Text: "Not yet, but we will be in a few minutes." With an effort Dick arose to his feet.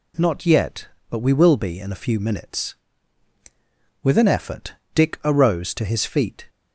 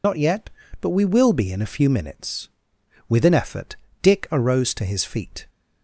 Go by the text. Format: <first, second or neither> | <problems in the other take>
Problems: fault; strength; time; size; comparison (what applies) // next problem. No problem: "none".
first | loses the start of "Not"; at 0.0 s; 55 ms // pauses between "effort" and "Dick"; slight; at 3.7 s; 0.26 s long; slight in the first